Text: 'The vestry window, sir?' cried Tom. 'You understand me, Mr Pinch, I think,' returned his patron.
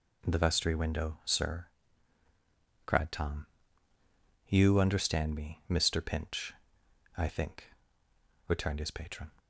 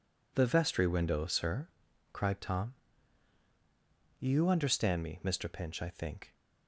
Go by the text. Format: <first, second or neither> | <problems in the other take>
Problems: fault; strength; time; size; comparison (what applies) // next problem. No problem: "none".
first | stops before "returned his patron"; at 6.3 s